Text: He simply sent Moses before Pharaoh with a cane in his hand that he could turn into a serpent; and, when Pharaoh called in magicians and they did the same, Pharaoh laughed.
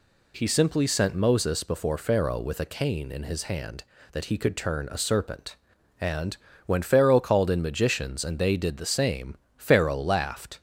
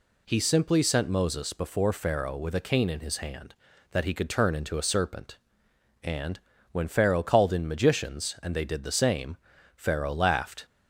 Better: second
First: skips "into"; at 4.9 s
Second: none

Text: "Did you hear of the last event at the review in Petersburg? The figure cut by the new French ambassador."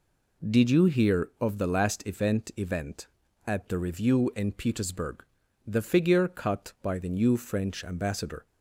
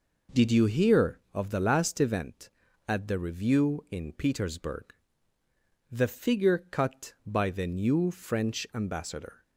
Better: second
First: says "event" twice; at 2.5 s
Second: none

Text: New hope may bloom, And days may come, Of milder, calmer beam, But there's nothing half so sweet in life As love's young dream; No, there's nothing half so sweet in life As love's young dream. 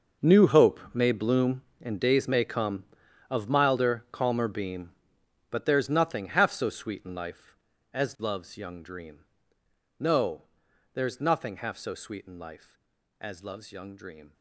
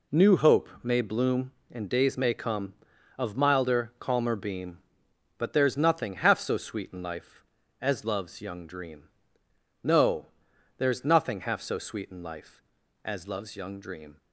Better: second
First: gets quieter; strong; throughout; 15.5 dB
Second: none

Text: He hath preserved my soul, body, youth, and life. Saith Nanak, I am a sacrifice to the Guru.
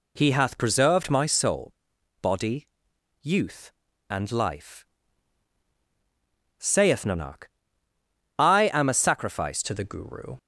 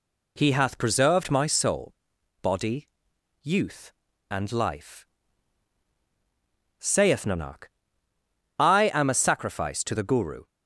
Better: second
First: changes voice at "to"; from 9.6 s on; 0.7 s long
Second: none

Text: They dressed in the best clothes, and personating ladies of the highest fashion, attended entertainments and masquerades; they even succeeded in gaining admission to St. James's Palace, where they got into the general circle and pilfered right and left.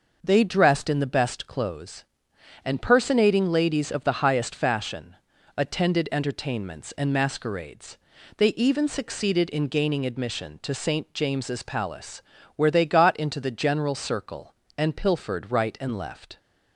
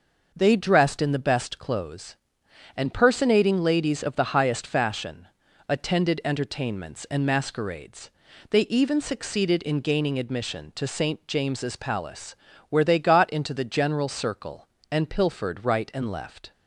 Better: neither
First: none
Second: none

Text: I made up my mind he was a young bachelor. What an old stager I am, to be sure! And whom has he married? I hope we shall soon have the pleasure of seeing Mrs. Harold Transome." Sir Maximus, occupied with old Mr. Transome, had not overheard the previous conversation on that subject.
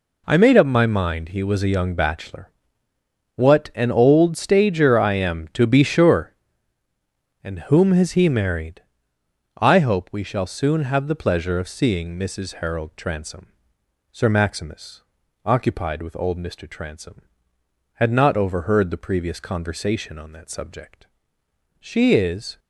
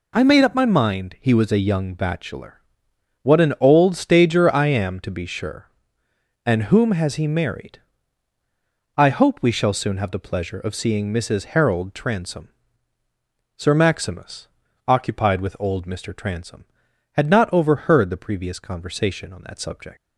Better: second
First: goes on to say "She is"; noticeable; from 21.8 s on; 0.78 s long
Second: none

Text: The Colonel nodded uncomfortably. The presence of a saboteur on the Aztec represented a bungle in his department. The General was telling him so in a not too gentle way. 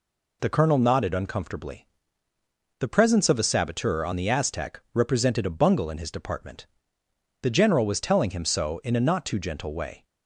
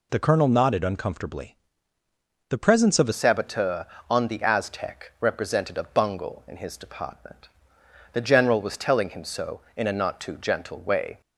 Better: first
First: none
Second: changes voice at "saboteur"; from 3.1 s on; 8.1 s long

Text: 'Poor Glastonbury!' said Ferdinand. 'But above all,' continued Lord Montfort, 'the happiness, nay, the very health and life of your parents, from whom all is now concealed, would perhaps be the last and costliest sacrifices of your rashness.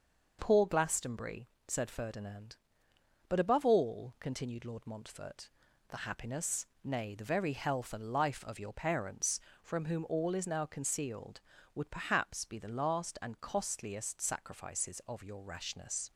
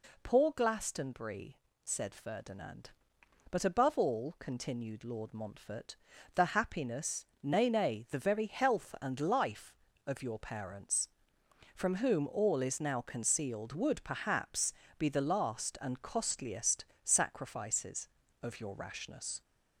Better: first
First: none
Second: says "nay" twice; at 7.6 s // pauses between "perhaps" and "be"; slight; at 14.7 s; 0.24 s long // pauses between "costliest" and "sacrifices"; slight; at 16.8 s; 0.18 s long

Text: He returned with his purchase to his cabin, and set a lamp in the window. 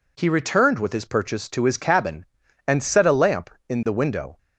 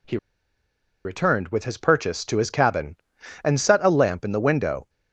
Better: first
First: none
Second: pauses between "He" and "returned"; noticeable; at 0.1 s; 0.87 s long

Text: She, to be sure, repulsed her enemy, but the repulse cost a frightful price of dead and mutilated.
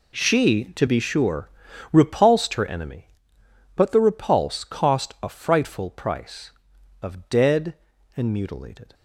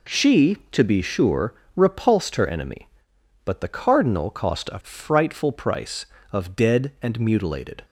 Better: first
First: none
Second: says "cardinal" for "repulse"; at 3.6 s

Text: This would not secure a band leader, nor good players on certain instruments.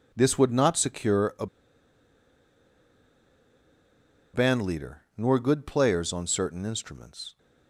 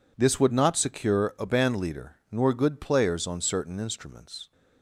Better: second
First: pauses between "a" and "band"; strong; at 1.4 s; 2.8 s long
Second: none

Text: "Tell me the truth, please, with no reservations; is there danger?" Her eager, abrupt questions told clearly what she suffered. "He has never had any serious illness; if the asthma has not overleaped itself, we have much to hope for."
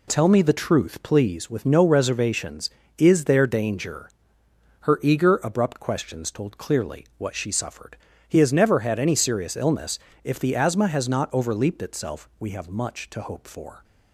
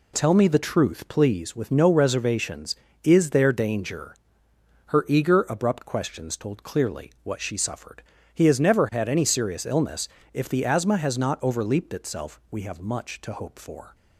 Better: neither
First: none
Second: none

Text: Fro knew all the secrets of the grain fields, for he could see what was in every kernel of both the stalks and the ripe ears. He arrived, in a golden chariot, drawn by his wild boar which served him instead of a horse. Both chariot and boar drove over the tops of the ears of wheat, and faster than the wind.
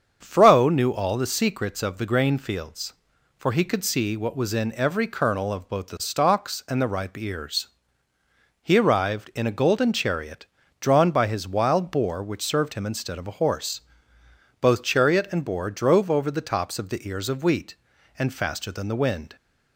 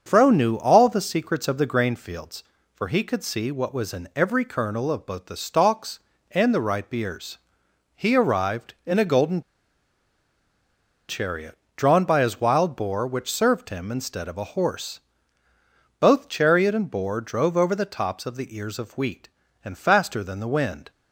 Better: first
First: starts louder than the rest; until 1.2 s; 7 dB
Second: starts louder than the rest; until 1.0 s; 7 dB // pauses between "golden" and "chariot"; strong; at 9.4 s; 1.6 s long

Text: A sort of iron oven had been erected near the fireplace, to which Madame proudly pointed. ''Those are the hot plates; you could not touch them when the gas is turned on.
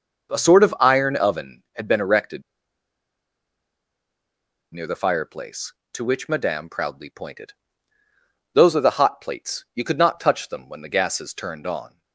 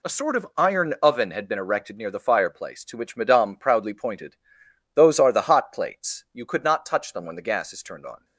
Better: second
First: pauses between "erected" and "near"; strong; at 2.4 s; 2.3 s long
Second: none

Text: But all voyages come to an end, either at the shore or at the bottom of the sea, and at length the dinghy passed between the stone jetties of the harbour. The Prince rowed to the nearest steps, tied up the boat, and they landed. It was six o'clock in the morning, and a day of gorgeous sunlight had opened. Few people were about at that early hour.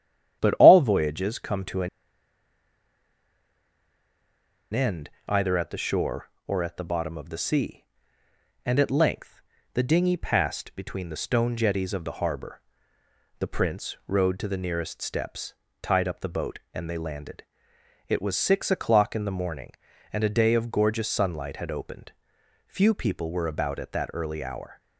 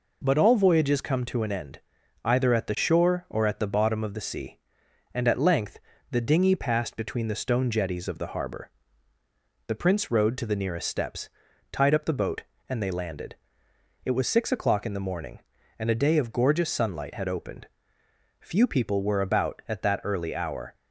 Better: second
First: starts louder than the rest; strong; until 1.4 s; 10.5 dB // pauses between "an" and "end"; strong; at 1.8 s; 2.8 s long // pauses between "length" and "the"; slight; at 9.4 s; 0.32 s long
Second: pauses between "length" and "the"; slight; at 5.7 s; 0.32 s long

